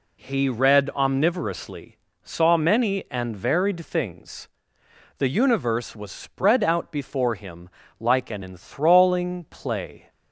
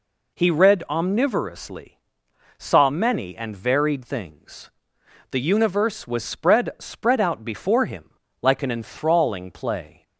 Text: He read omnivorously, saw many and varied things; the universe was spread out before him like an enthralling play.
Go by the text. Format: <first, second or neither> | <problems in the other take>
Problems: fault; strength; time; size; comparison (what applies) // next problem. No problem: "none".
first | says "spread" twice; at 6.7 s // pauses between "him" and "like"; slight; at 8.1 s; 0.32 s long; slight in the first